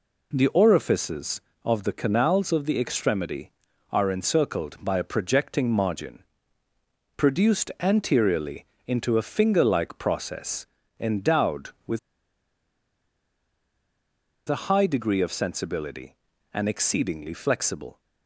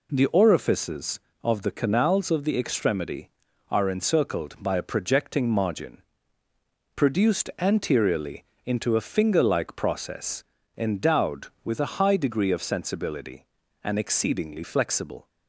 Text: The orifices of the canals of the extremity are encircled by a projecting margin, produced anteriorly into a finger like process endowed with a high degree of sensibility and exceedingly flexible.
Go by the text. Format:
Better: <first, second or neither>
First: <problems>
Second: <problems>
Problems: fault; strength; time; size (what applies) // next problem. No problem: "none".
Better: second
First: pauses between "anteriorly" and "into"; slight; at 8.6 s; 0.22 s long // pauses between "process" and "endowed"; slight; at 10.6 s; 0.32 s long // pauses between "with" and "a"; strong; at 11.9 s; 2.4 s long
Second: pauses between "anteriorly" and "into"; slight; at 8.4 s; 0.22 s long // pauses between "process" and "endowed"; slight; at 10.4 s; 0.32 s long